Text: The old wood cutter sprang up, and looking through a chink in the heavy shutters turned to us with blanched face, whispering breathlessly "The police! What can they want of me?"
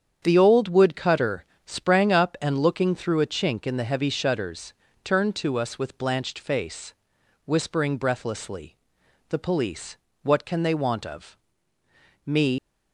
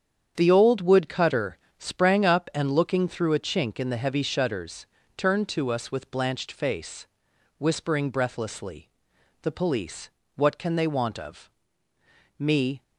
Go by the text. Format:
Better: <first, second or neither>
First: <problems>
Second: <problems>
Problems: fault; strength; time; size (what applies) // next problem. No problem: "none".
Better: second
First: starts louder than the rest; strong; until 1.2 s; 8 dB // pauses between "cutter" and "sprang"; slight; at 1.4 s; 0.22 s long // pauses between "shutters" and "turned"; slight; at 4.7 s; 0.30 s long // pauses between "breathlessly" and "The"; noticeable; at 8.7 s; 0.50 s long // pauses between "of" and "me"; noticeable; at 11.3 s; 0.90 s long // leaves "me" unfinished; at 12.5 s; 110 ms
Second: starts louder than the rest; strong; until 1.3 s; 8 dB // pauses between "cutter" and "sprang"; slight; at 1.5 s; 0.22 s long // pauses between "shutters" and "turned"; slight; at 4.8 s; 0.30 s long // pauses between "breathlessly" and "The"; noticeable; at 8.9 s; 0.50 s long // pauses between "of" and "me"; noticeable; at 11.4 s; 0.90 s long